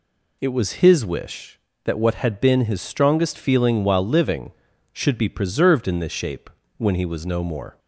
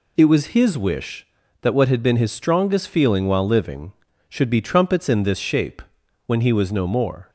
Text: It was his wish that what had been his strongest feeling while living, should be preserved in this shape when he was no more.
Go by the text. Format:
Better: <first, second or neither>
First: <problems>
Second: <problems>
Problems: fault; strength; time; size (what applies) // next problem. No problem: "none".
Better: first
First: pauses between "shape" and "when"; slight; at 6.5 s; 0.26 s long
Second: says "trumpets" for "preserved"; at 4.6 s // pauses between "shape" and "when"; at 5.8 s; 0.44 s long